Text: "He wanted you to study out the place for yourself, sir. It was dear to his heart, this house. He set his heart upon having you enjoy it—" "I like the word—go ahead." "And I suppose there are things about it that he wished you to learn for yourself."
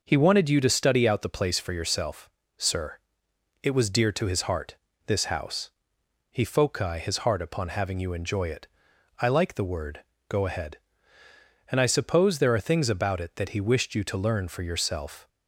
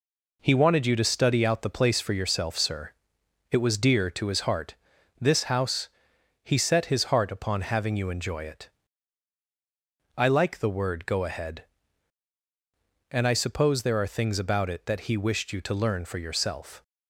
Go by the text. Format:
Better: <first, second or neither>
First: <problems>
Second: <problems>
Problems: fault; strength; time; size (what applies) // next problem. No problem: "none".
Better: second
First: says "foci" for "set"; at 6.4 s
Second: none